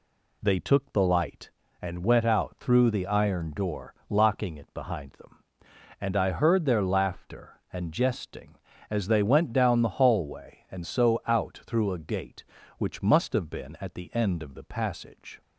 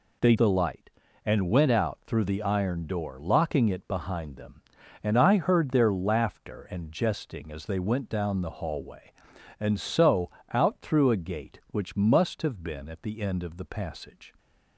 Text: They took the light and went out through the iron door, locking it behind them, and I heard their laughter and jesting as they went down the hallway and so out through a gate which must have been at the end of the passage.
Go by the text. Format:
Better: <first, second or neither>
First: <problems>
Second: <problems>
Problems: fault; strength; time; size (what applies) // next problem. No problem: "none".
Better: first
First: none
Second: skips "took"; at 0.3 s // pauses between "so" and "out"; slight; at 10.2 s; 0.24 s long